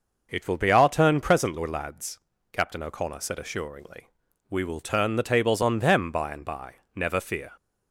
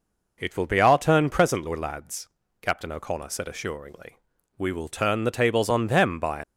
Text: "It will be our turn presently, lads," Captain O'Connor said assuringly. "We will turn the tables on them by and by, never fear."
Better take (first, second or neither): first